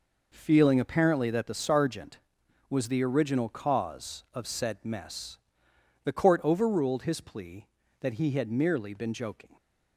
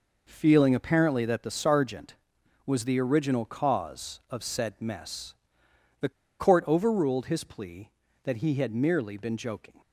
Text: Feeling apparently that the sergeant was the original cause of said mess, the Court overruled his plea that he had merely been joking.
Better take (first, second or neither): first